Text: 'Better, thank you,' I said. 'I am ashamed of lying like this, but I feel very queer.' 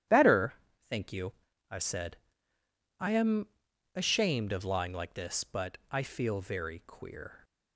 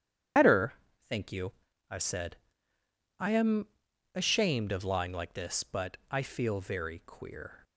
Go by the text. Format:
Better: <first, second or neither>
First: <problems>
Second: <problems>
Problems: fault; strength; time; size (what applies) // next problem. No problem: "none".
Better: first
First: starts louder than the rest; strong; until 1.8 s; 11.5 dB // pauses between "am" and "ashamed"; noticeable; at 3.4 s; 0.48 s long // pauses between "but" and "I"; slight; at 5.7 s; 0.16 s long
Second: loses the start of "Better"; at 0.3 s; 65 ms // starts louder than the rest; strong; until 2.1 s; 10.5 dB // pauses between "am" and "ashamed"; noticeable; at 3.6 s; 0.48 s long // pauses between "but" and "I"; slight; at 5.9 s; 0.16 s long